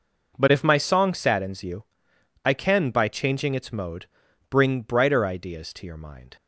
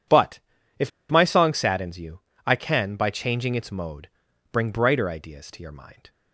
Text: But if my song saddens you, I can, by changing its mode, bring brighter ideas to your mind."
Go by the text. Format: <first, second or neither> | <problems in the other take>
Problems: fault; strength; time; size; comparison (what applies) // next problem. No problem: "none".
first | pauses between "But" and "if"; at 0.3 s; 0.40 s long // pauses between "if" and "my"; slight; at 0.9 s; 0.19 s long